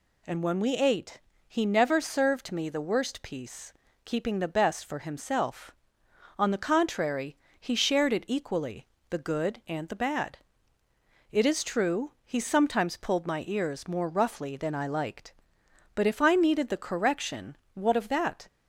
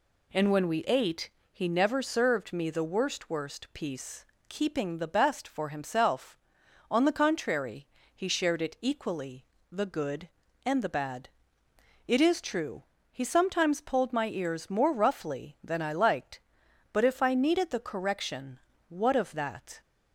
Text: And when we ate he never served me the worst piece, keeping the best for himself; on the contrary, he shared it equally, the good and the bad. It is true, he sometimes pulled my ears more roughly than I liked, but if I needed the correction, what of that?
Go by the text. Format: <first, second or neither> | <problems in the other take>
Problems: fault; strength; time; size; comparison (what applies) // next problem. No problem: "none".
first | pauses between "ate" and "he"; slight; at 1.3 s; 0.22 s long; slight in the first // says "worst" twice; at 3.2 s